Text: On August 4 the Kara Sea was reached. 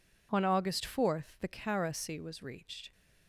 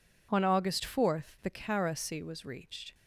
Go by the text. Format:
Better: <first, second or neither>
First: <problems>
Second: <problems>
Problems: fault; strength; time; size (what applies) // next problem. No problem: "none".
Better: neither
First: none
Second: none